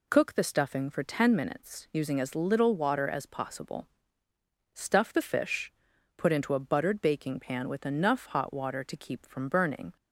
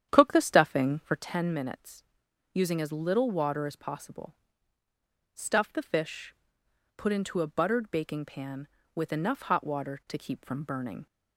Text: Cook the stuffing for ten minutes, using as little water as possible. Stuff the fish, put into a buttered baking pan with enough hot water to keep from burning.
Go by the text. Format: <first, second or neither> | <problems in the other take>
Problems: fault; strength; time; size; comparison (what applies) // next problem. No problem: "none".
first | starts louder than the rest; strong; until 1.2 s; 9.5 dB